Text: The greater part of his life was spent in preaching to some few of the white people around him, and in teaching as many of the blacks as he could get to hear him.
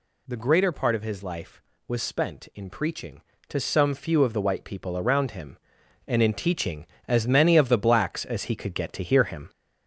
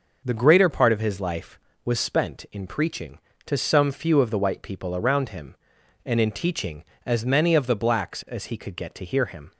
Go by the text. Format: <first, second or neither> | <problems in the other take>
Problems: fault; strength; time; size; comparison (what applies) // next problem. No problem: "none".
second | gets louder; noticeable; throughout; 4.5 dB